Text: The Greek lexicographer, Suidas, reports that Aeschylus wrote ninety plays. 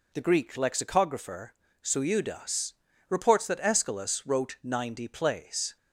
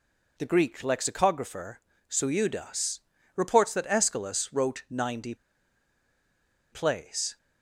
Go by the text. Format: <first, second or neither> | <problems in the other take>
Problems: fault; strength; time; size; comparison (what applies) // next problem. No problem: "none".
first | pauses between "ninety" and "plays"; strong; at 5.3 s; 1.3 s long